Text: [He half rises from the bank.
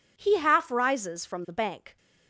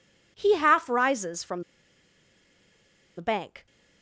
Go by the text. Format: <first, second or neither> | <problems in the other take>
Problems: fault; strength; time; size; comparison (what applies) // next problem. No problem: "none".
first | pauses between "from" and "the"; strong; at 1.6 s; 1.5 s long